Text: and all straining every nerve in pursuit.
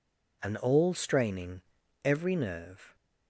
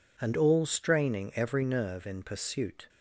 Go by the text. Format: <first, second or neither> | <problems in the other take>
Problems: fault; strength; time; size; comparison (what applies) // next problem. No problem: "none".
second | pauses between "straining" and "every"; at 1.6 s; 0.44 s long // stops before "in pursuit"; at 2.9 s